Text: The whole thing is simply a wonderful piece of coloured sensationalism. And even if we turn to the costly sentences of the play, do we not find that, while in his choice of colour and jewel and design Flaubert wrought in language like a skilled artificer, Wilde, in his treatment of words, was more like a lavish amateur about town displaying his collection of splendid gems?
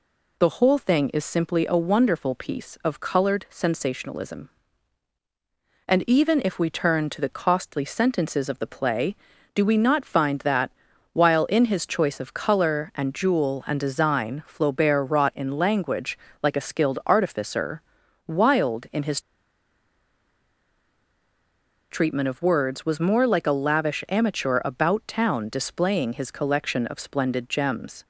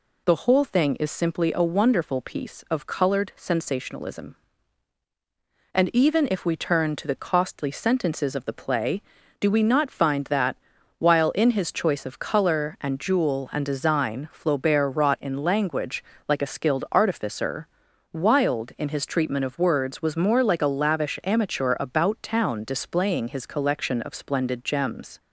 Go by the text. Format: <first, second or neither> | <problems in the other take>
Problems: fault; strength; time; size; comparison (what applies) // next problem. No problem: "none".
second | pauses between "language" and "like"; slight; at 16.1 s; 0.24 s long; slight in the second // pauses between "his" and "treatment"; strong; at 19.1 s; 2.7 s long